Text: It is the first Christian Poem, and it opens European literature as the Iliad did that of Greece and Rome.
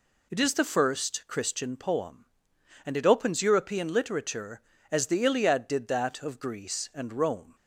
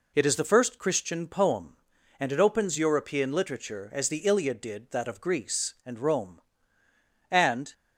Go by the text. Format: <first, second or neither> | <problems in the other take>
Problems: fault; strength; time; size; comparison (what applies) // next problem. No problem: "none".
first | goes on to say "And"; slight; from 7.2 s on; 0.44 s long